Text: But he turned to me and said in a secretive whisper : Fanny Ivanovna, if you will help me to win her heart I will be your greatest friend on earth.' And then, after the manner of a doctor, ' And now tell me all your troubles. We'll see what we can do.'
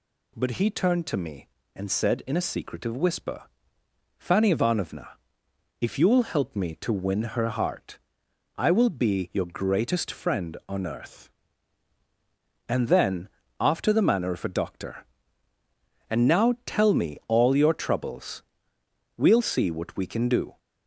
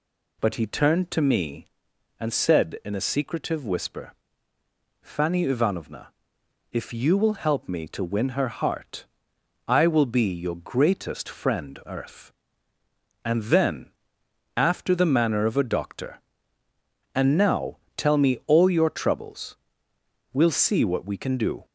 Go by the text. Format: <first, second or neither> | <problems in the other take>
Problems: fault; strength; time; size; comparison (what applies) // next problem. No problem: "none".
first | pauses between "heart" and "I"; noticeable; at 9.0 s; 0.62 s long; noticeable in the first // skips "on"; at 11.8 s // pauses between "now" and "tell"; slight; at 17.7 s; 0.18 s long